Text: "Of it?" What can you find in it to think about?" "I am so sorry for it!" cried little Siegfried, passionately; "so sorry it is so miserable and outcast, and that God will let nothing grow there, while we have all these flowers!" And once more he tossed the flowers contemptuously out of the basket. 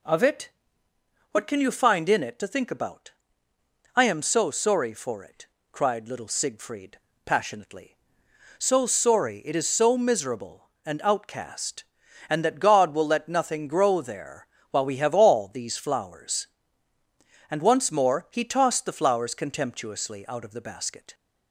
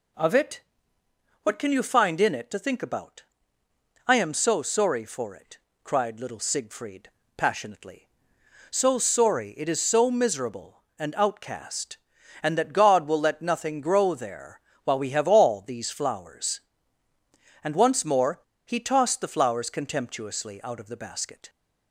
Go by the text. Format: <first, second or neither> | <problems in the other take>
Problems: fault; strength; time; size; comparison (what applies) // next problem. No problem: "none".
first | pauses between "more" and "he"; slight; at 18.3 s; 0.28 s long